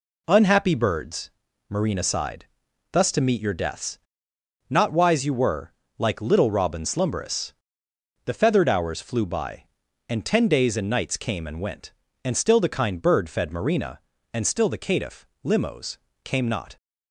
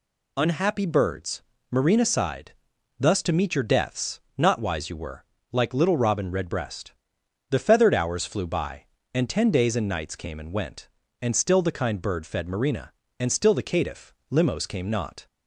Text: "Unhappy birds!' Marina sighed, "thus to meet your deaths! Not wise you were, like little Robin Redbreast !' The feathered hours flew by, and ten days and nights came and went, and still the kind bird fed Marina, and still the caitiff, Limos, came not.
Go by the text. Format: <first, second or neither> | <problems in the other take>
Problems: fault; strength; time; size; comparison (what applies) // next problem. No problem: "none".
second | says "Slumberous" for "Redbreast"; at 6.8 s